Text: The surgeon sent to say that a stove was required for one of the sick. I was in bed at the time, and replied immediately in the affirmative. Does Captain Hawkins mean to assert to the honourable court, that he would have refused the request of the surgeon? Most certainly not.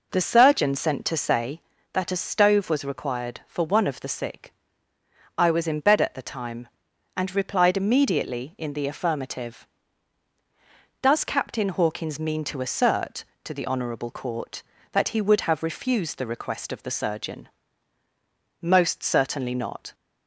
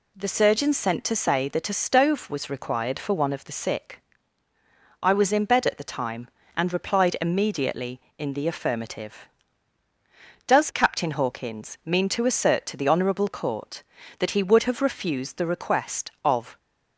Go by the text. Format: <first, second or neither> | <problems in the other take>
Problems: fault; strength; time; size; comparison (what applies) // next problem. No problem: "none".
first | stops before "the surgeon Most certainly not"; at 16.5 s